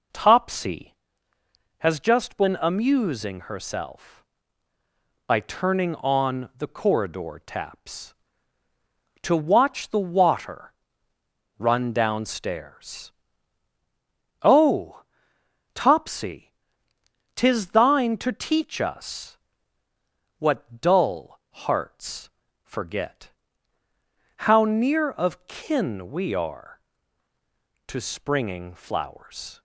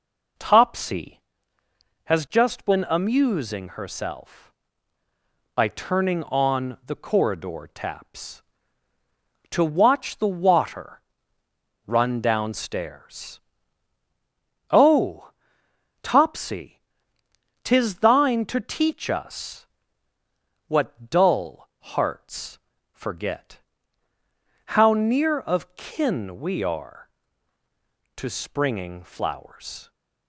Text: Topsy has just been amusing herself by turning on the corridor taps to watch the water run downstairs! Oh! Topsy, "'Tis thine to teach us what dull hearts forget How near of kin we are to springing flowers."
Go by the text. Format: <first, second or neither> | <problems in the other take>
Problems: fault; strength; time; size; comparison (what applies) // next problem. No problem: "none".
neither | pauses between "water" and "run"; noticeable; the same in both // pauses between "us" and "what"; the same in both // pauses between "hearts" and "forget"; slight; the same in both // pauses between "forget" and "How"; the same in both